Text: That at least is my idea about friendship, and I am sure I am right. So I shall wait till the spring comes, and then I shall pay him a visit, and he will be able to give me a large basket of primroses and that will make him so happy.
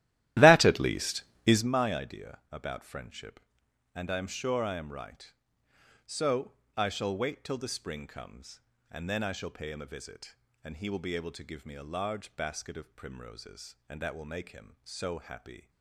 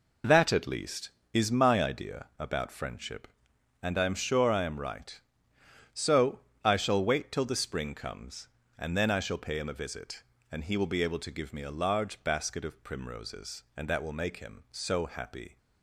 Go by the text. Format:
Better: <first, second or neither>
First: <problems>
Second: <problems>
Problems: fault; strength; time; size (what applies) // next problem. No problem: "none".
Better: second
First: starts louder than the rest; strong; until 1.7 s; 14.5 dB // pauses between "So" and "I"; slight; at 6.5 s; 0.24 s long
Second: pauses between "So" and "I"; slight; at 6.3 s; 0.24 s long